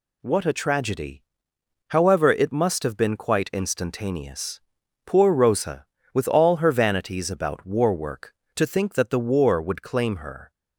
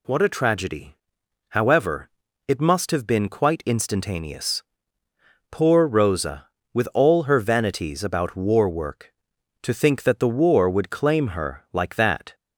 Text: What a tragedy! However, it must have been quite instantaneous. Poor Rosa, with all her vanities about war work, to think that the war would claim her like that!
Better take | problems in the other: second | stops before "like that"; at 10.5 s

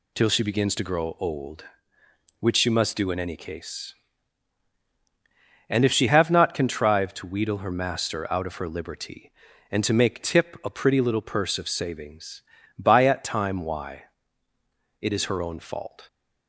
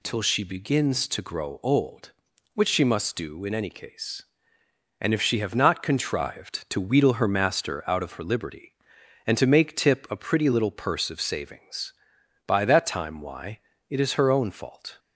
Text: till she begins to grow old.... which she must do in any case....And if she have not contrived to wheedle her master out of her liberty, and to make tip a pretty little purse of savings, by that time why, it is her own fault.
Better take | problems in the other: second | says "at" for "that"; at 13.0 s

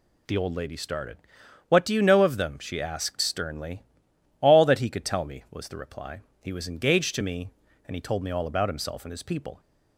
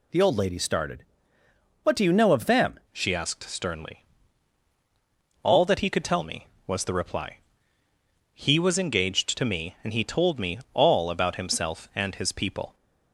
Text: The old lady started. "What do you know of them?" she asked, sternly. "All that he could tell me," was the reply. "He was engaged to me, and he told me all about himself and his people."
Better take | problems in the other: first | changes voice at "she"; from 2.9 s on; 9.8 s long // pauses between "me" and "all"; slight; at 10.5 s; 0.16 s long

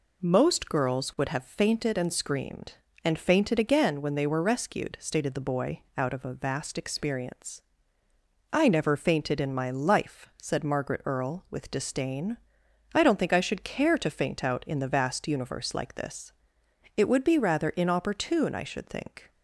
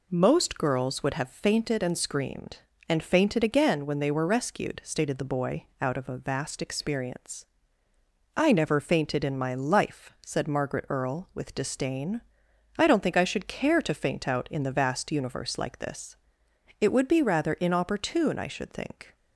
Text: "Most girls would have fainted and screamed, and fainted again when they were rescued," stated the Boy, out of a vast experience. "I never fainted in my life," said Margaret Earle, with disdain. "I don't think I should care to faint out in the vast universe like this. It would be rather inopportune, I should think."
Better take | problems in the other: neither | none

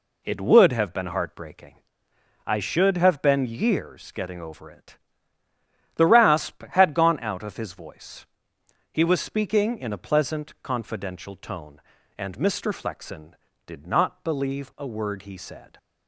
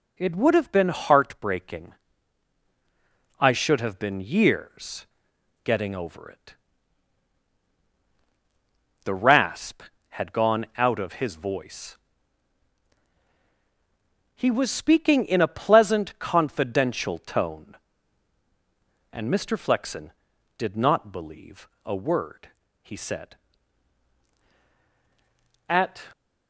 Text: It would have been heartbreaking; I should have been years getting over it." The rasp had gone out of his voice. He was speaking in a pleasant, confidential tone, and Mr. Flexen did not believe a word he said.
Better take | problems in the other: first | pauses between "years" and "getting"; noticeable; at 5.0 s; 0.58 s long // pauses between "believe" and "a"; slight; at 21.6 s; 0.16 s long // pauses between "word" and "he"; slight; at 22.4 s; 0.34 s long // goes on to say "At"; slight; from 25.6 s on; 0.40 s long

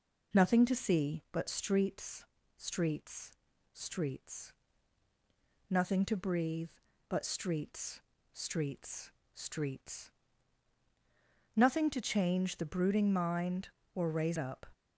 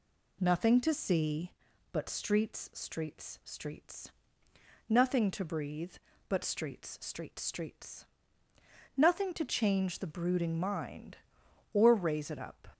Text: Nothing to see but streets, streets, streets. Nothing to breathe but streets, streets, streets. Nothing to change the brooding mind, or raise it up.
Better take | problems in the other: second | skips "it"; at 14.3 s

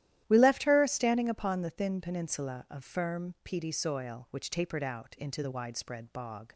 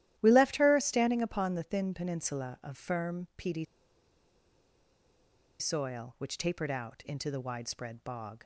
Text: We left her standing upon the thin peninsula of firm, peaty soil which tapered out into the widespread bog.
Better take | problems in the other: first | starts louder than the rest; strong; until 1.1 s; 13 dB; strong in the first // pauses between "peaty" and "soil"; strong; at 3.6 s; 1.9 s long

